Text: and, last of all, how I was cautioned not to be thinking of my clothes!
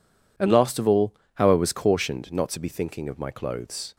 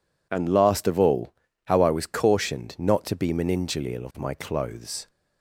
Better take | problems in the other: first | says "meningeal" for "thinking"; at 3.3 s

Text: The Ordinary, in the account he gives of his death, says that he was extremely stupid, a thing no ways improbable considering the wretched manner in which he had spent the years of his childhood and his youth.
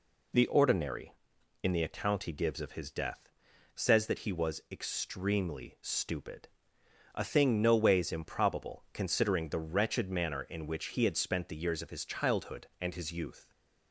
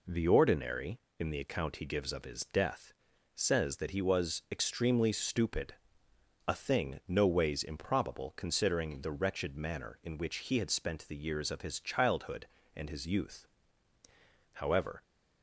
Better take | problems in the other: first | goes on to say "However"; from 14.5 s on; 0.50 s long

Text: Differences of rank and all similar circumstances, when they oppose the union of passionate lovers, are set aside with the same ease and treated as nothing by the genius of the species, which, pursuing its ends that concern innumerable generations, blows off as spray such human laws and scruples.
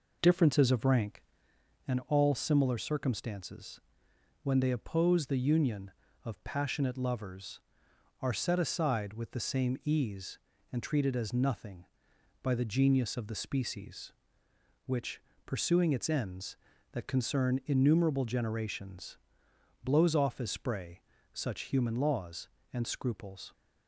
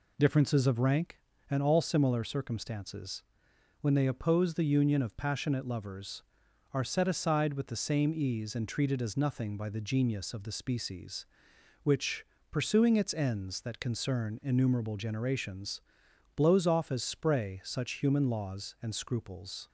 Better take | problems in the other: second | starts louder than the rest; noticeable; until 1.5 s; 4.5 dB // pauses between "spray" and "such"; slight; at 21.0 s; 0.32 s long

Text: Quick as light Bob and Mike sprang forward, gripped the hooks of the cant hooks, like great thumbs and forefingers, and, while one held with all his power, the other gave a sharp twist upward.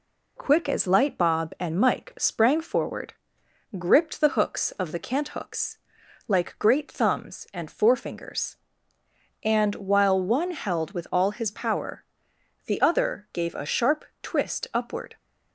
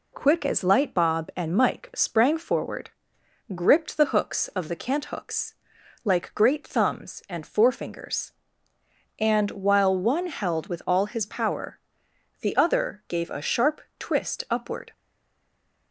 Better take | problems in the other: first | pauses between "sharp" and "twist"; slight; at 13.8 s; 0.18 s long; slight in the first // stays silent after the last word; from 14.9 s on; 1.0 s long

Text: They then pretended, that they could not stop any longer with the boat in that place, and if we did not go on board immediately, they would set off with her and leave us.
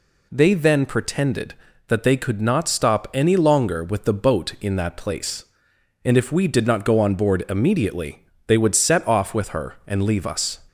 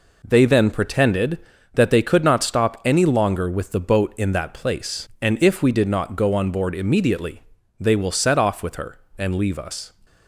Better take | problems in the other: first | says "will" for "would"; at 7.9 s

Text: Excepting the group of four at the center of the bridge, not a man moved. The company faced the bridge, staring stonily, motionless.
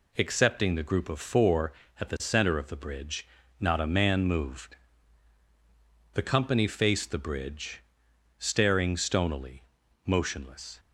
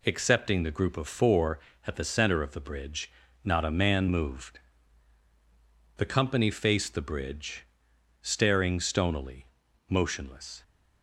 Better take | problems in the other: neither | none

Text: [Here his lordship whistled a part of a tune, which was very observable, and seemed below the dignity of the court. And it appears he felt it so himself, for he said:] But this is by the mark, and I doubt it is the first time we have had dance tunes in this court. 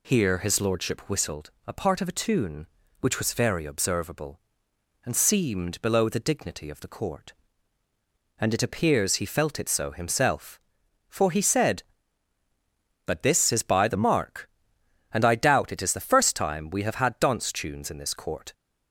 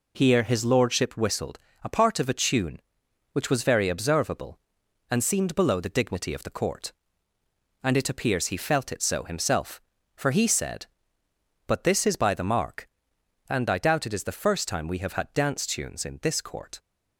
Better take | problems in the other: neither | pauses between "whistled" and "a"; slight; the same in both

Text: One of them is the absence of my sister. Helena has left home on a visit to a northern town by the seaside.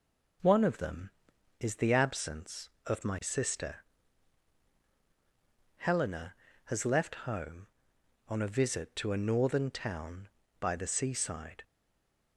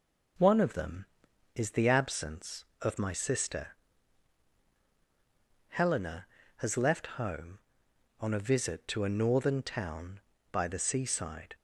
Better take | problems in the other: second | stays silent after the last word; slight; from 11.6 s on; 0.7 s long

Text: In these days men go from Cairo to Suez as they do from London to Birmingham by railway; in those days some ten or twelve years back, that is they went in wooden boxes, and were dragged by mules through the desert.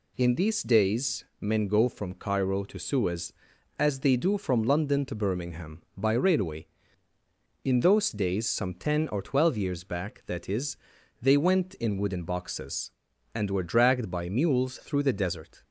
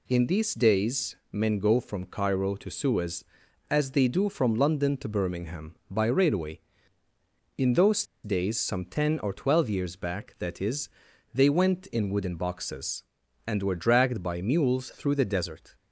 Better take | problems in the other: first | pauses between "days" and "men"; slight; at 1.1 s; 0.16 s long; slight in the first // pauses between "those" and "days"; slight; at 8.0 s; 0.20 s long // pauses between "is" and "they"; noticeable; at 10.8 s; 0.46 s long; noticeable in the first

